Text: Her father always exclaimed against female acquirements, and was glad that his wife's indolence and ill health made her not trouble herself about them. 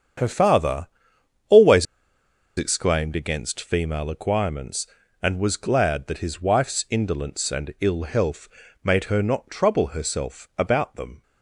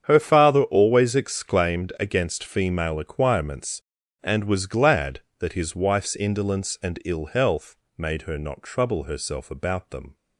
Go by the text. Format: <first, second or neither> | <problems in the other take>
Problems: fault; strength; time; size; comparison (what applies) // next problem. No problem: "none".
second | starts louder than the rest; strong; until 1.7 s; 8 dB; strong in the second // pauses between "father" and "always"; noticeable; at 0.8 s; 0.60 s long // pauses between "always" and "exclaimed"; noticeable; at 1.8 s; 0.72 s long // pauses between "health" and "made"; slight; at 8.4 s; 0.34 s long; slight in the second